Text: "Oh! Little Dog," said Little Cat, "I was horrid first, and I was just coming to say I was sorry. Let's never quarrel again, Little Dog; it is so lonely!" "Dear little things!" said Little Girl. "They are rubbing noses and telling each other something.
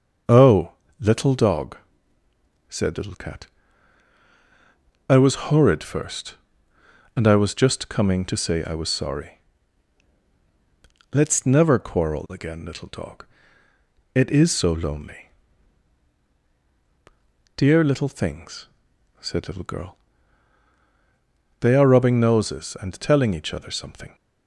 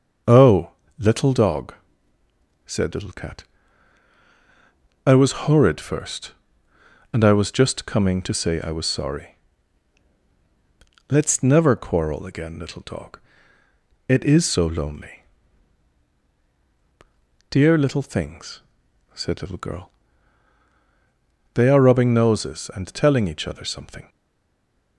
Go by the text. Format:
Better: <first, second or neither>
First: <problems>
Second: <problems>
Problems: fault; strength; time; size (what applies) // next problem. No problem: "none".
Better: first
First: starts louder than the rest; until 1.5 s; 6.5 dB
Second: starts louder than the rest; until 1.5 s; 6.5 dB // stays silent after the last word; slight; from 24.0 s on; 0.9 s long